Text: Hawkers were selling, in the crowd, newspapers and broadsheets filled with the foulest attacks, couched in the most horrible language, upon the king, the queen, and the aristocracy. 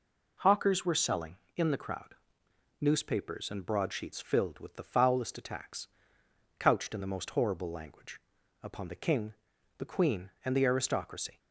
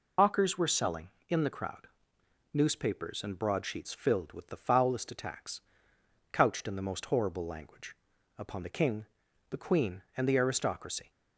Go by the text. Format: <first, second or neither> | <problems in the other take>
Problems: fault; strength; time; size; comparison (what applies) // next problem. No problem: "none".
first | loses the start of "Hawkers"; at 0.1 s; 60 ms